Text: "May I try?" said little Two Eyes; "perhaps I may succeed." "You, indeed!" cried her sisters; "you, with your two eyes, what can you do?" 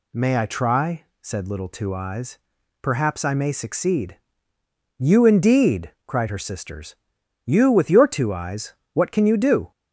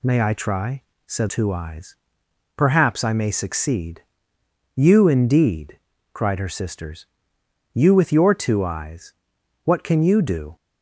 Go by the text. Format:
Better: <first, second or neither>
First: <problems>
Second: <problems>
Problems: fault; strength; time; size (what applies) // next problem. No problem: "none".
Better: first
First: none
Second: skips "little"; at 1.2 s